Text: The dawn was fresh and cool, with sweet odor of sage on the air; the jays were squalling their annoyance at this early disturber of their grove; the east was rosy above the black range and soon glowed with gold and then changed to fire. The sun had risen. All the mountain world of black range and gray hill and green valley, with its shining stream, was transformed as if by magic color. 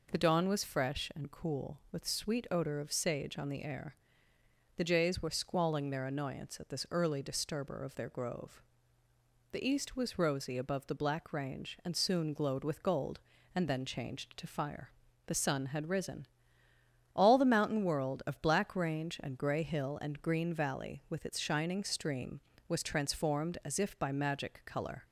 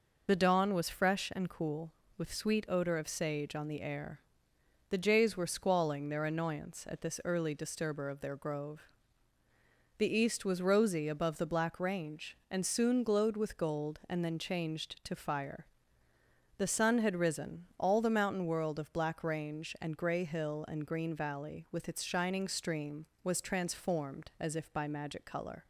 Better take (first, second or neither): first